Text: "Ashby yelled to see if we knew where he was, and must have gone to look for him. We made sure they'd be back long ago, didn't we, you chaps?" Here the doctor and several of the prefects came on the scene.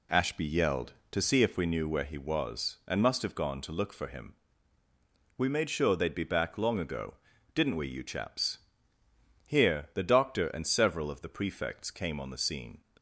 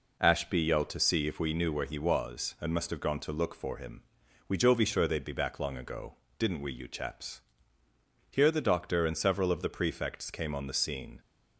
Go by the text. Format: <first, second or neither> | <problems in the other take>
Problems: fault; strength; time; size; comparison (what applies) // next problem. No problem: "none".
first | says "jovi" for "made"; at 4.5 s